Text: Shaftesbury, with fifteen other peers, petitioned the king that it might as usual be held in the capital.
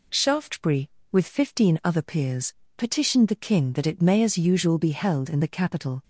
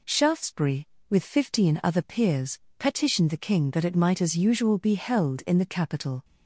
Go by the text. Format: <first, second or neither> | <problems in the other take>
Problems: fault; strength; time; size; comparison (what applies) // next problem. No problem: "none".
second | says "may" for "might"; at 4.0 s